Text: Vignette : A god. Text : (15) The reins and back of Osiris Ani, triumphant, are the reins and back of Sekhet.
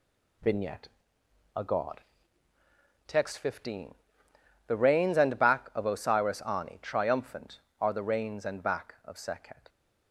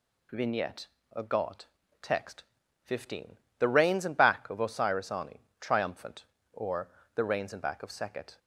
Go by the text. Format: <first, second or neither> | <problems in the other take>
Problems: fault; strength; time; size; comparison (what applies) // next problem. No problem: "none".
first | says "or" for "are"; at 6.5 s